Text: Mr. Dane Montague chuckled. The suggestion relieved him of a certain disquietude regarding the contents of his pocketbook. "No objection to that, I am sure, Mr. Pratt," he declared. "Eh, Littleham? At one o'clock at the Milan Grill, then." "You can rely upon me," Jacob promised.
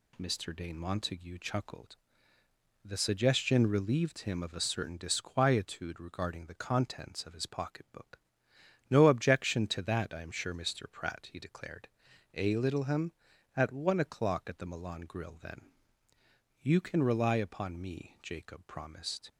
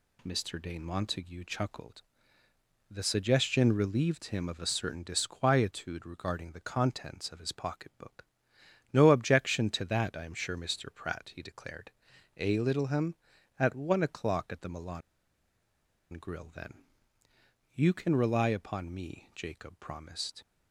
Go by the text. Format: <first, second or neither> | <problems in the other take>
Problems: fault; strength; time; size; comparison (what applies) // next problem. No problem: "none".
first | pauses between "Milan" and "Grill"; at 15.0 s; 1.1 s long